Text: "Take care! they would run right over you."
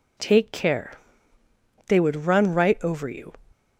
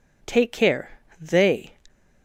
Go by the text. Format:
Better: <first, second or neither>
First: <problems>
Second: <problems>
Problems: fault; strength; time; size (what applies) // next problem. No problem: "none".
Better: first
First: none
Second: stops before "would run right over you"; at 1.8 s